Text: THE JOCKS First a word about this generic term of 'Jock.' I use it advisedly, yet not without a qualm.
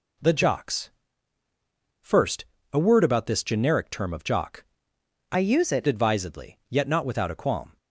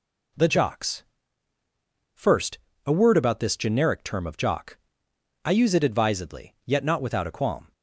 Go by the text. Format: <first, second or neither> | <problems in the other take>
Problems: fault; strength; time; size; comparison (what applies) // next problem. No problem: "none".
second | pauses between "JOCKS" and "First"; at 0.8 s; 1.1 s long; also in the second // pauses between "First" and "a"; slight; at 2.4 s; 0.28 s long; slight in the second // changes voice from "use" to "it"; from 5.3 to 5.8 s; 0.5 s long